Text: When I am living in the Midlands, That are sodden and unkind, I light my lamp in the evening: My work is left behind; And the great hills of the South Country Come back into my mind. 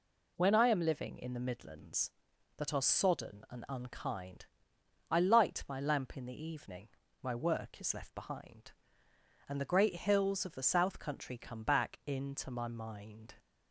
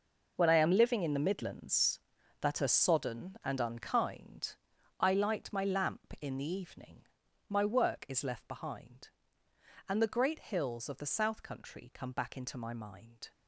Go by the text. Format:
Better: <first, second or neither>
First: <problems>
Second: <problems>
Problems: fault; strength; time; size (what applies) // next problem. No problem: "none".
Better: first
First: none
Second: gets quieter; strong; throughout; 12.5 dB